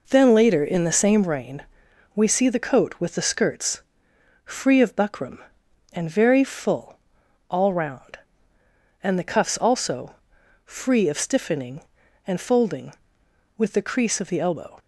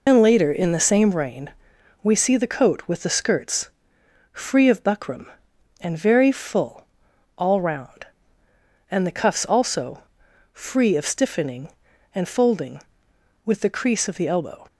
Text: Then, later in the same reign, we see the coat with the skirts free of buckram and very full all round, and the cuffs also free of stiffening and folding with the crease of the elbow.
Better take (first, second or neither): first